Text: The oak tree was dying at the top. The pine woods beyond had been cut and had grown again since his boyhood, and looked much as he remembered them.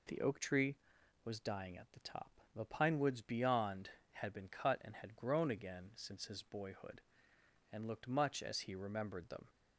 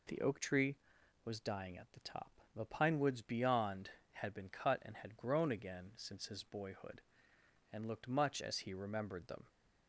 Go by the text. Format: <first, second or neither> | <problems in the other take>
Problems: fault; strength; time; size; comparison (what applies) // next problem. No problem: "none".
neither | none